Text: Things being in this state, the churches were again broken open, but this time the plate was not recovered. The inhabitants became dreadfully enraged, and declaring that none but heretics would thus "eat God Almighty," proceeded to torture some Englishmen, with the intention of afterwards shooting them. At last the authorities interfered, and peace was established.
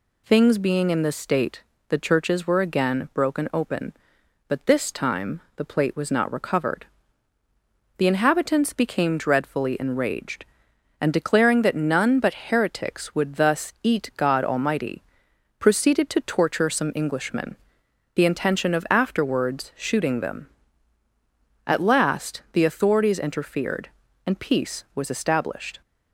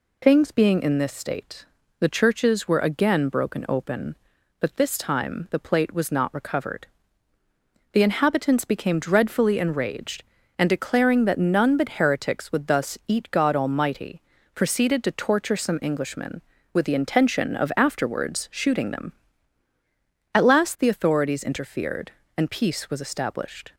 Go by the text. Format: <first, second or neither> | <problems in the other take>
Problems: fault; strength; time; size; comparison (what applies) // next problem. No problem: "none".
second | pauses between "time" and "the"; slight; at 5.4 s; 0.16 s long // skips "with"; at 17.8 s